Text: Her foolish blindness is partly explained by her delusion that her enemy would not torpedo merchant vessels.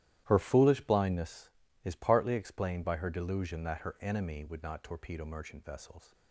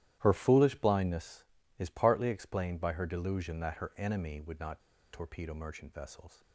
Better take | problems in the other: first | starts louder than the rest; strong; until 1.2 s; 13 dB; strong in the first // pauses between "not" and "torpedo"; slight; at 4.8 s; 0.32 s long

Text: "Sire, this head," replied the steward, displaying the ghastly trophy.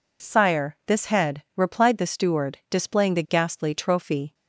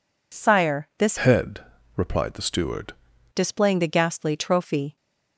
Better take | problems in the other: first | changes voice from "head" to "steward"; from 1.1 to 2.9 s; 1.8 s long

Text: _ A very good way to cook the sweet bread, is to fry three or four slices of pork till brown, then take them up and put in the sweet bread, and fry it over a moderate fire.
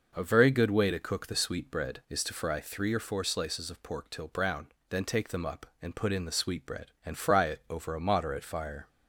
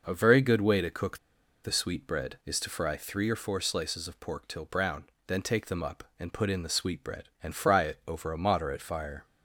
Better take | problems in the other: first | pauses between "cook" and "the"; noticeable; at 1.1 s; 0.47 s long

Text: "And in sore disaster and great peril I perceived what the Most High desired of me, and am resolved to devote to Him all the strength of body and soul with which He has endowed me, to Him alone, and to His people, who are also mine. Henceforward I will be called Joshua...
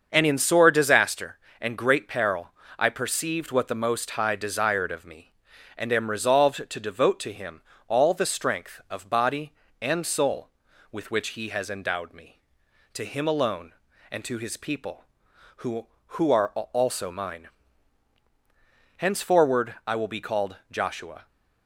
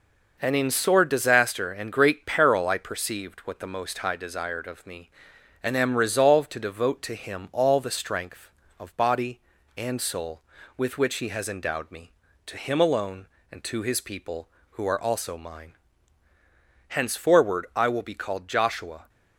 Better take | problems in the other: second | starts louder than the rest; until 1.1 s; 6.5 dB // pauses between "peril" and "I"; slight; at 2.5 s; 0.26 s long // pauses between "Him" and "all"; slight; at 7.6 s; 0.26 s long // says "who" twice; at 16.1 s

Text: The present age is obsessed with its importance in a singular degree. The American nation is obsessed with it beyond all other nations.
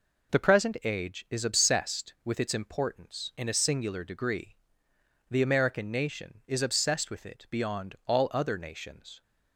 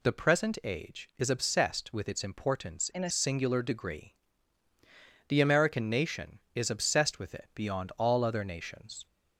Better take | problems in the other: first | changes voice from "in" to "a"; from 2.9 to 3.1 s; 0.2 s long

